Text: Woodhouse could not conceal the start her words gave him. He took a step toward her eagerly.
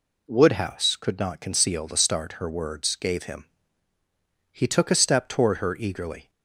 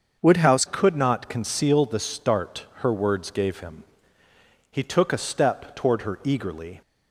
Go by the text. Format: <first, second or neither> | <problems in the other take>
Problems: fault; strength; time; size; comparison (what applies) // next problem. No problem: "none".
first | starts louder than the rest; until 1.2 s; 6.5 dB // changes voice at "could"; from 0.7 s on; 6.1 s long